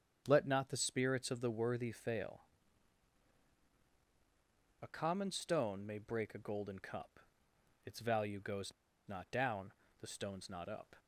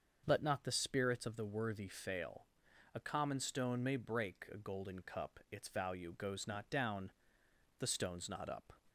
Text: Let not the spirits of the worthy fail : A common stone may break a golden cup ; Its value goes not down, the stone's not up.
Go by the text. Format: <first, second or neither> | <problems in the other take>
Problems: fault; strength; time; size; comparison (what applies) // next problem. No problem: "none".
second | starts louder than the rest; strong; until 1.2 s; 8 dB; also in the second // pauses between "goes" and "not"; slight; at 8.7 s; 0.35 s long